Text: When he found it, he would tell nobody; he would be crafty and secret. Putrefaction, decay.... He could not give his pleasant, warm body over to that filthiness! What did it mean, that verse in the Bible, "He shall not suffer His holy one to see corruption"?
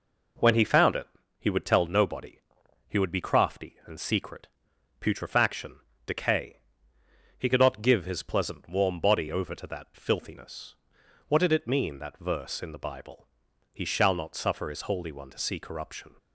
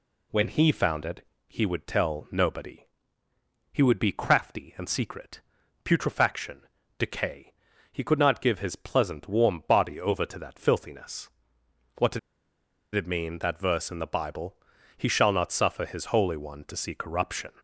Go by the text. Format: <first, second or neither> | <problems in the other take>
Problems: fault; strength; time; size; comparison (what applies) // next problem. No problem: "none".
first | pauses between "did" and "it"; noticeable; at 12.1 s; 0.75 s long